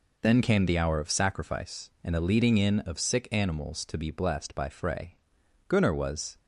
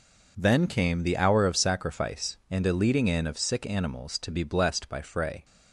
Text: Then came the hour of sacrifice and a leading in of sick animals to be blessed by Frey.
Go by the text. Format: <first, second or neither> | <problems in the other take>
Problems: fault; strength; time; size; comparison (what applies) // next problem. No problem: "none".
second | goes on to say "Gunnar was"; noticeable; from 5.6 s on; 0.70 s long